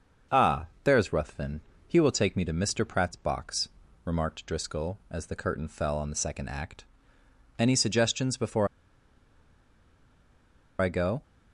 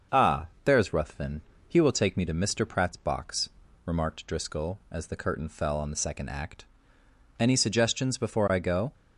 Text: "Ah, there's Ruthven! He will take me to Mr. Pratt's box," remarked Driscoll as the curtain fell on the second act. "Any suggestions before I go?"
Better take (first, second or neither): second